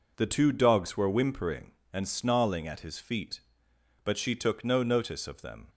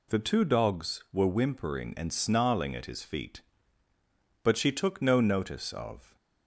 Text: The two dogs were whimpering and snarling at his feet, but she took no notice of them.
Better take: first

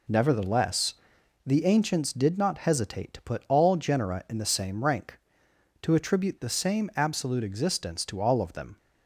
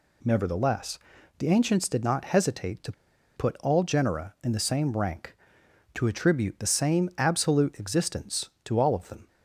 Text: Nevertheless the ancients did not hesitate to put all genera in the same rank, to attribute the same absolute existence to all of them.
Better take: first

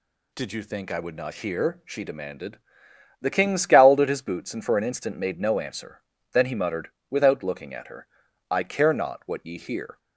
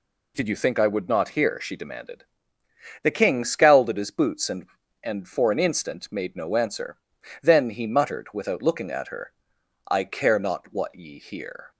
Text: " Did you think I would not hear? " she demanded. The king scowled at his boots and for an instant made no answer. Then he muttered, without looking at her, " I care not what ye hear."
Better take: first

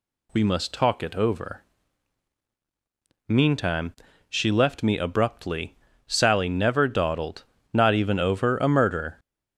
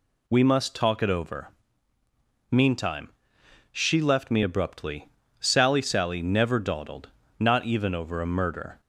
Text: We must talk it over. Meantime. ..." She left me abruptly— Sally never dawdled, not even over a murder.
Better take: first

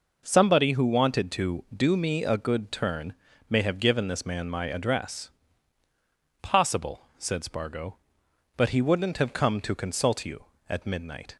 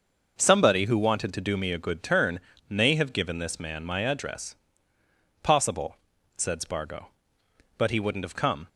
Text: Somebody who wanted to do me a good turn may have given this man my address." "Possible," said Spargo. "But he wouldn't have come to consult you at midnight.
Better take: first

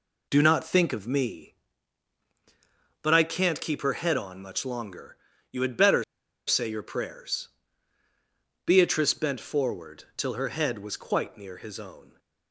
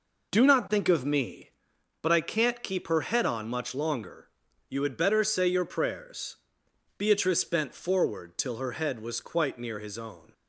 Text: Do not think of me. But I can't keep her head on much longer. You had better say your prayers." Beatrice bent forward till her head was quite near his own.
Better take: second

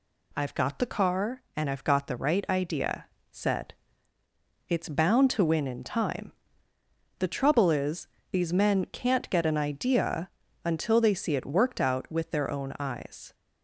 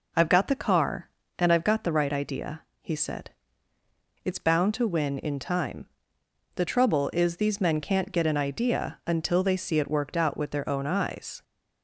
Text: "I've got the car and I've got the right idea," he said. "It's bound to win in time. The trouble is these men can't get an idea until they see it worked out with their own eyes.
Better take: second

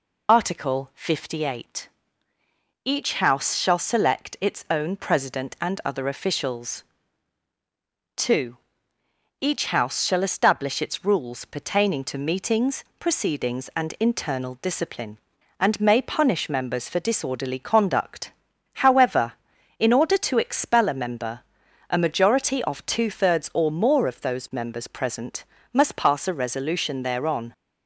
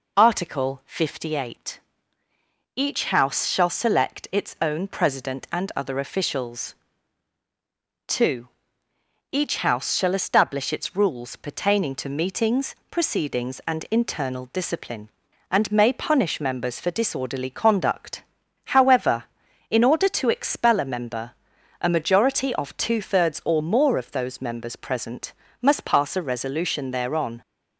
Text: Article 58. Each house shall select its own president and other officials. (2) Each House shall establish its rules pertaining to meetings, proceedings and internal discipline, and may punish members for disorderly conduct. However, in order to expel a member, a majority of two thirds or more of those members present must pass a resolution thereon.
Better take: second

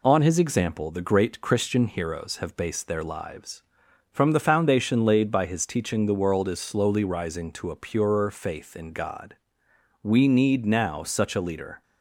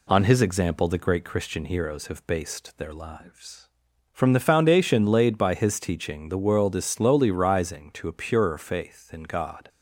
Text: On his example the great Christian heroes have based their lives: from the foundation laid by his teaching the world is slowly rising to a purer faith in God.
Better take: second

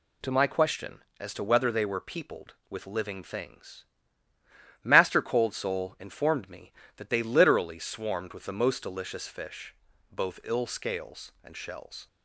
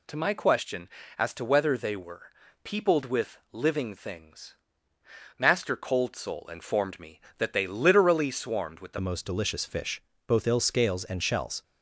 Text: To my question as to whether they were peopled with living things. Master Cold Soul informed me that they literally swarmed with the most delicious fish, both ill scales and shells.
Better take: first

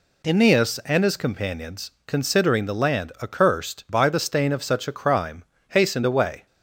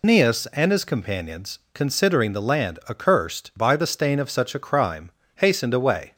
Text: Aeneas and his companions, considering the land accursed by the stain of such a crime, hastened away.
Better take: first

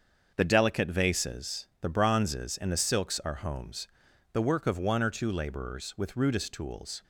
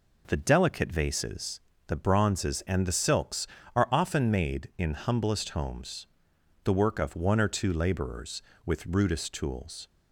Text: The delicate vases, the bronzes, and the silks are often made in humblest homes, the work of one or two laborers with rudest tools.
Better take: second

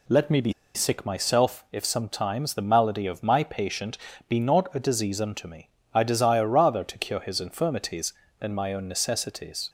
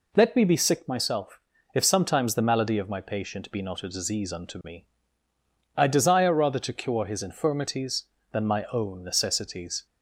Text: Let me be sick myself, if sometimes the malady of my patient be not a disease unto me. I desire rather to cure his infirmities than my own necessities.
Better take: second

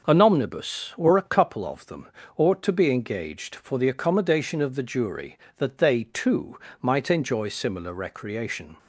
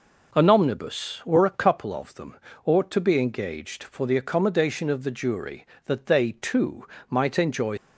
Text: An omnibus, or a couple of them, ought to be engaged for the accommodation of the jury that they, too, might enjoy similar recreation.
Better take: first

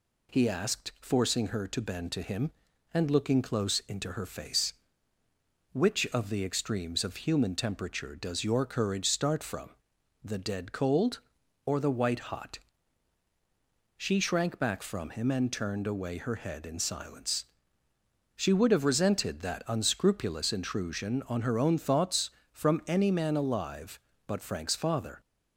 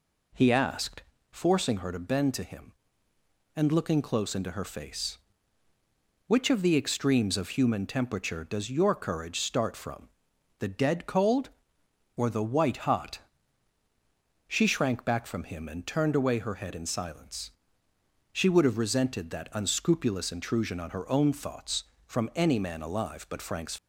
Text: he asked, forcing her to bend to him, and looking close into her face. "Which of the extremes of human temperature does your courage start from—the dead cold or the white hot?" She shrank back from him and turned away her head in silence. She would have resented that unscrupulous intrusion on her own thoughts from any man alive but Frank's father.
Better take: first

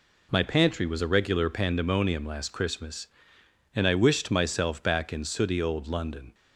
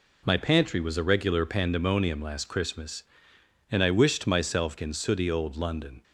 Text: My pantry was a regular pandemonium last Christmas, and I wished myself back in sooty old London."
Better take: first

